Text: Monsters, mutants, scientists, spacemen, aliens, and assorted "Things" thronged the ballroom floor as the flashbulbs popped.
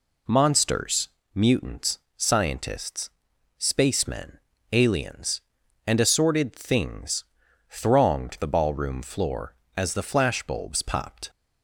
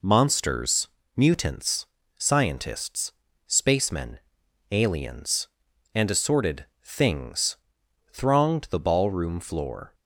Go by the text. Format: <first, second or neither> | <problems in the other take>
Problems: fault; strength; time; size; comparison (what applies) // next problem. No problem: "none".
first | pauses between "assorted" and "Things"; slight; at 6.6 s; 0.18 s long // pauses between "Things" and "thronged"; noticeable; at 7.5 s; 0.56 s long; noticeable in the first // stops before "as the flashbulbs popped"; at 9.9 s